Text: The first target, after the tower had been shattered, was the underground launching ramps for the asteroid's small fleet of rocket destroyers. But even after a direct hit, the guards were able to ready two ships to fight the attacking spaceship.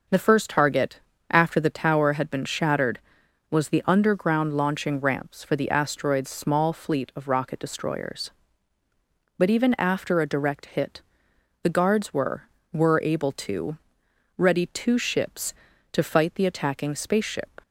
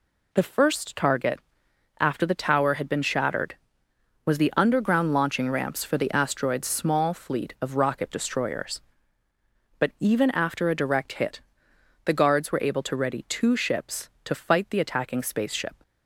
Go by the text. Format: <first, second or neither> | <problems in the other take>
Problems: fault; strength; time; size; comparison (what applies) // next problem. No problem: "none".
second | starts louder than the rest; noticeable; until 1.4 s; 6 dB // says "were" twice; at 12.7 s // pauses between "to" and "ready"; noticeable; at 13.7 s; 0.58 s long